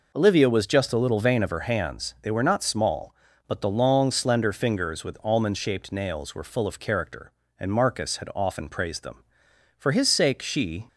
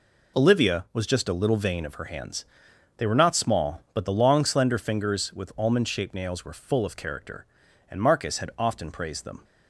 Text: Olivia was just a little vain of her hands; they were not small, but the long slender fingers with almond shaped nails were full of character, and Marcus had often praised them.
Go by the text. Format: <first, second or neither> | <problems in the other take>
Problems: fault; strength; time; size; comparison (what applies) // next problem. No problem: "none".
second | goes on to say "For his sake she"; noticeable; from 9.7 s on; 1.0 s long